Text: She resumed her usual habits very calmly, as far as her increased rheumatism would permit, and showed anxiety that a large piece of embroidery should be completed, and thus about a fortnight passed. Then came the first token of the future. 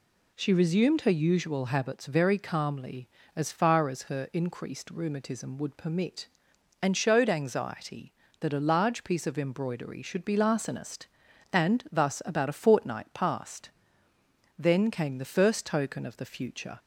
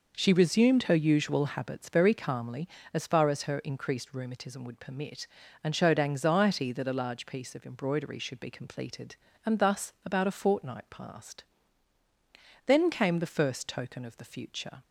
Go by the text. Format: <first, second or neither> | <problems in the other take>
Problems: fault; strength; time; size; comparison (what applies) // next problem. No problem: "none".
second | says "larcenist" for "completed"; at 10.3 s